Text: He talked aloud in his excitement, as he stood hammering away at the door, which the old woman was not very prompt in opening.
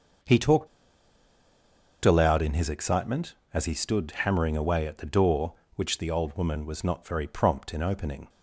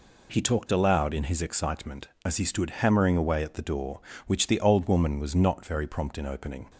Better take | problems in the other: second | starts louder than the rest; until 2.6 s; 6.5 dB // pauses between "talked" and "aloud"; strong; at 0.6 s; 1.3 s long

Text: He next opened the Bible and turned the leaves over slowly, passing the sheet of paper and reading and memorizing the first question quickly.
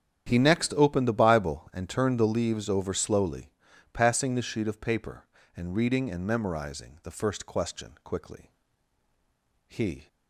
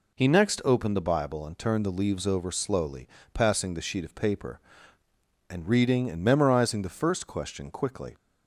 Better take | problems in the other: second | starts louder than the rest; strong; until 1.3 s; 9 dB // goes on to say "He"; slight; from 9.6 s on; 0.38 s long

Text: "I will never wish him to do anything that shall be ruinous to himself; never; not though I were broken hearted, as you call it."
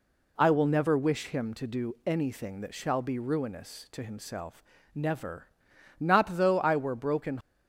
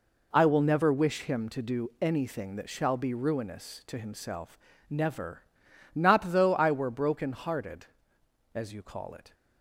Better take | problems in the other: second | stops before "hearted as you call it"; at 7.4 s

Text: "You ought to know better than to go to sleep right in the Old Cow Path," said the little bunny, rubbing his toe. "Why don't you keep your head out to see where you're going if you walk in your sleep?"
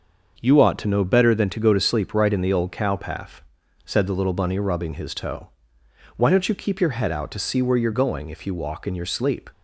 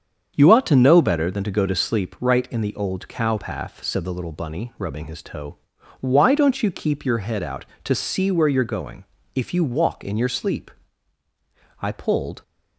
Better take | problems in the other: first | starts louder than the rest; strong; until 1.3 s; 7.5 dB; also in the first // pauses between "going" and "if"; slight; at 9.0 s; 0.32 s long // goes on to say "I pulled"; from 11.8 s on; 0.60 s long

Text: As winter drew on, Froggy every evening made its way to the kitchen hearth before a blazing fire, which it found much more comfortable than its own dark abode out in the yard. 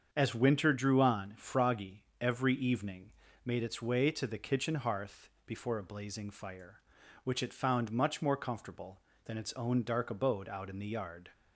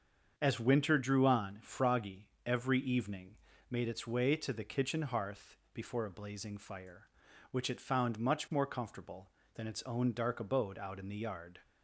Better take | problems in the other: neither | starts louder than the rest; the same in both // pauses between "Froggy" and "every"; slight; the same in both // pauses between "evening" and "made"; slight; the same in both // pauses between "hearth" and "before"; slight; the same in both

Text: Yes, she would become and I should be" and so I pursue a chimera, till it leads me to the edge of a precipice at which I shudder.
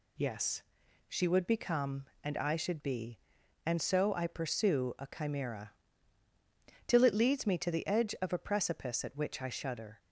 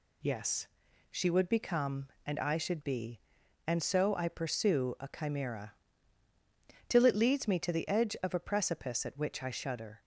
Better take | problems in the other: neither | none

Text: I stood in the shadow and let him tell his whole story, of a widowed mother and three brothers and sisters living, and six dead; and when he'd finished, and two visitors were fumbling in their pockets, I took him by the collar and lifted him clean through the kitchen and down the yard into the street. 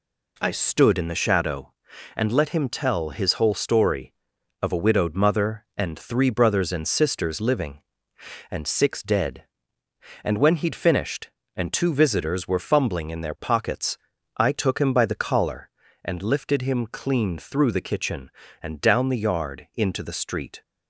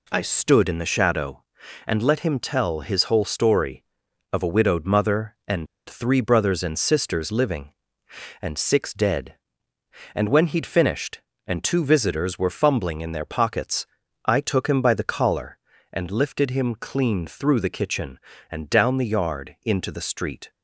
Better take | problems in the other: first | pauses between "and" and "three"; slight; at 5.6 s; 0.21 s long

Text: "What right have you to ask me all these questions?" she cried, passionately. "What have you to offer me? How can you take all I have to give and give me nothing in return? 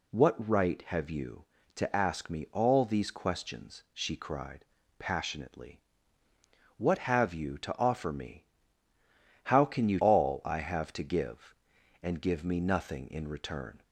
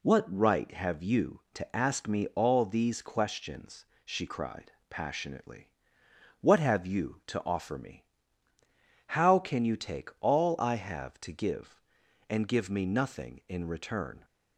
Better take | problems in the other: second | skips "take"; at 9.9 s

